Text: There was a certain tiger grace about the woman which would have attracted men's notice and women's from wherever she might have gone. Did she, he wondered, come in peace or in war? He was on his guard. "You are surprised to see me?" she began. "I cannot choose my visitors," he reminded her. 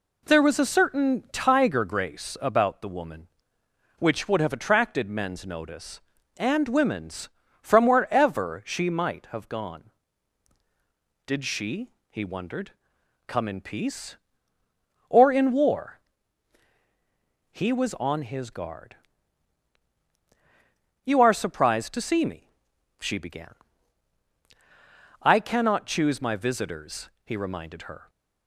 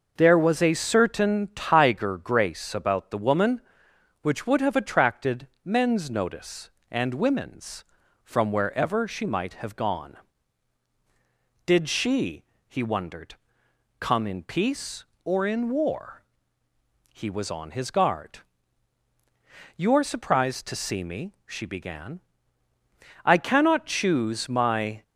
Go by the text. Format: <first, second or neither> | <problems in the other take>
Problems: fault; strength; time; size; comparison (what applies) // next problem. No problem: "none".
first | pauses between "attracted" and "men's"; slight; at 5.4 s; 0.16 s long // stops before "visitors he reminded her"; at 25.0 s